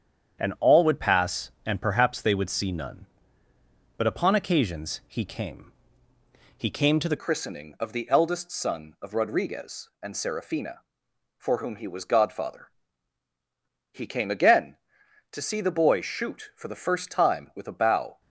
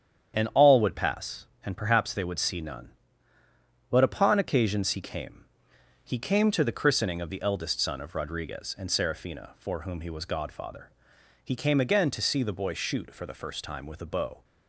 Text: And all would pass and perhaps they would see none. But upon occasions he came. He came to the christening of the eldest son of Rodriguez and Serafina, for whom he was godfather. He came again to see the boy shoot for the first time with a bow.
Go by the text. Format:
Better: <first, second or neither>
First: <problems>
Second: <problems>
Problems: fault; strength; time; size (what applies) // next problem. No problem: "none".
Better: second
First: starts louder than the rest; strong; until 1.4 s; 8 dB // changes voice at "christening"; from 7.1 s on; 11.1 s long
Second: starts louder than the rest; strong; until 1.3 s; 8.5 dB